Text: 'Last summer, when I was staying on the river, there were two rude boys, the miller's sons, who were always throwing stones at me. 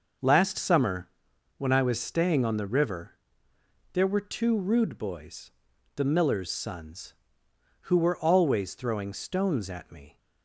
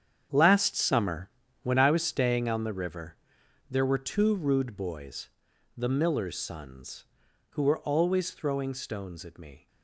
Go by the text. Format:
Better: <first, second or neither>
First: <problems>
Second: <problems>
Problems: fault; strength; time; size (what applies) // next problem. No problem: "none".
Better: first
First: none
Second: gets quieter; strong; throughout; 12 dB